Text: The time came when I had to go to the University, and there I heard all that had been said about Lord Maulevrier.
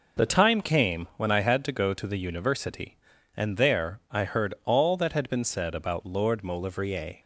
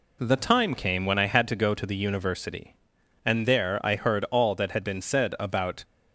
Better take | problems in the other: first | stops before "Lord Maulevrier"; at 5.8 s

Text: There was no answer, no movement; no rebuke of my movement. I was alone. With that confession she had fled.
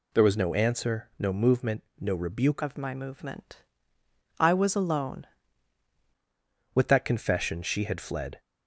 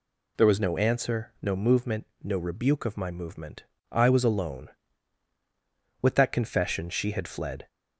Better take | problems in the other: second | changes voice from "of" to "alone"; from 2.6 to 5.2 s; 2.6 s long

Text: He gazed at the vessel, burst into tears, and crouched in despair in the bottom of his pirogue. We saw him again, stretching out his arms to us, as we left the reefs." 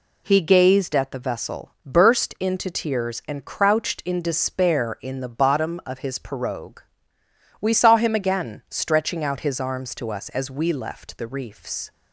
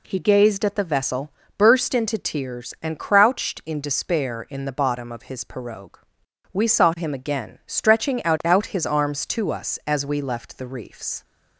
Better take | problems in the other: first | says "out" twice; at 8.4 s

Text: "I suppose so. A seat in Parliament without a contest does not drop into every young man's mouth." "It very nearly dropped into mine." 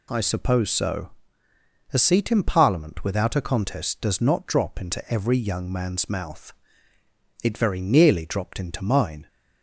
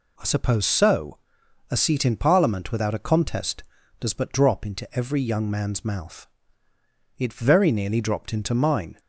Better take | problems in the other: first | says "but" for "not"; at 4.1 s

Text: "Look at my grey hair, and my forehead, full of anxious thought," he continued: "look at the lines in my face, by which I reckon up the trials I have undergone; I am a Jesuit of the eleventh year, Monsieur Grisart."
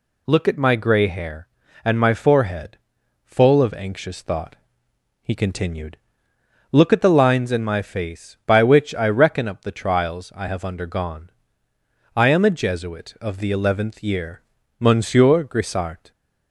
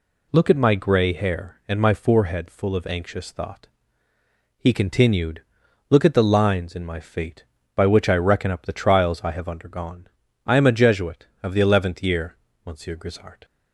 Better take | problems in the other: first | says "fate" for "face"; at 6.9 s

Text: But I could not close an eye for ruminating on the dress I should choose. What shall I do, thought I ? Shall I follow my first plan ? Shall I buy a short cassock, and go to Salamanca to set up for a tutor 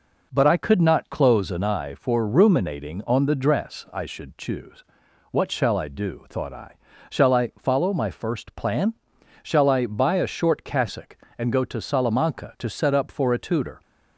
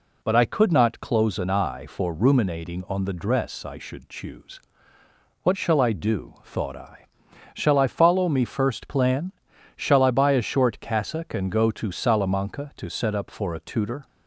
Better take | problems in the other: first | says "me" for "my"; at 8.2 s

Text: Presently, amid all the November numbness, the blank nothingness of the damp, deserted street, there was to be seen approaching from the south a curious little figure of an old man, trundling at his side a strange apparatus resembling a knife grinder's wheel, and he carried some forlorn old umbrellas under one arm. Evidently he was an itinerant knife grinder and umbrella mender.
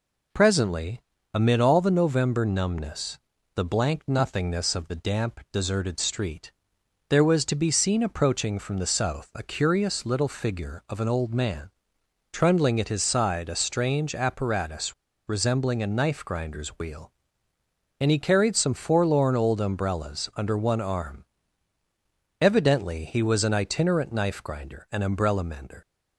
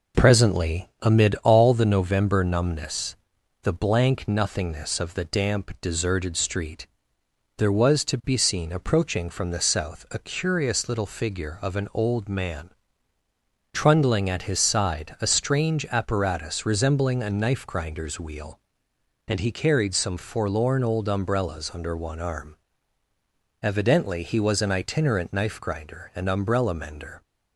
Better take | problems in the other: second | pauses between "apparatus" and "resembling"; slight; at 14.9 s; 0.33 s long

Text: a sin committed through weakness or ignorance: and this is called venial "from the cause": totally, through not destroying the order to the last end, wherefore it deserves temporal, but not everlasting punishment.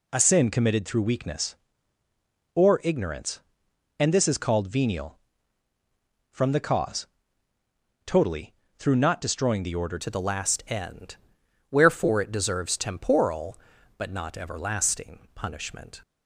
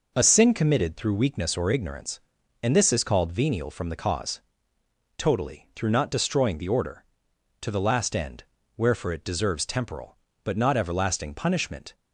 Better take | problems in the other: second | changes voice at "to"; from 9.9 s on; 6.1 s long

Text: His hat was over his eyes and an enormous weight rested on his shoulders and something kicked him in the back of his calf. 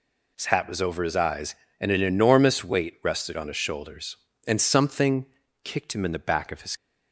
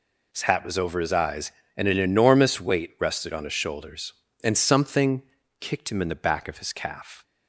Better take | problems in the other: second | pauses between "something" and "kicked"; slight; at 5.2 s; 0.36 s long; slight in the second // stops before "calf"; at 6.7 s

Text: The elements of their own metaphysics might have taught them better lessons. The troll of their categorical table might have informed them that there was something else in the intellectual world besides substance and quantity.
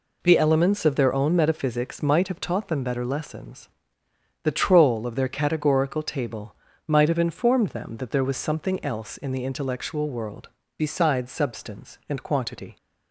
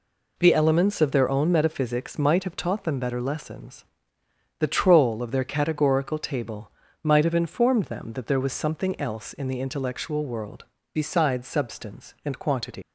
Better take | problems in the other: first | pauses between "table" and "might"; slight; at 6.7 s; 0.32 s long; slight in the first // pauses between "world" and "besides"; slight; at 10.6 s; 0.28 s long; slight in the first // leaves "quantity" unfinished; at 12.8 s; 100 ms

